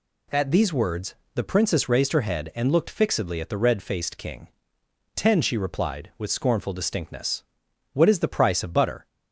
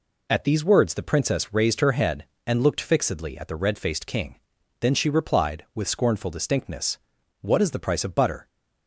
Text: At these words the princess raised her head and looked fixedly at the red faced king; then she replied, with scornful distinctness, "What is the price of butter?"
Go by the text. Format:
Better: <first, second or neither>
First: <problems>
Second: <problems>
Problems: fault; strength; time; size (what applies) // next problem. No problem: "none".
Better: second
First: pauses between "words" and "the"; slight; at 1.1 s; 0.18 s long // says "ten" for "then"; at 5.1 s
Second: none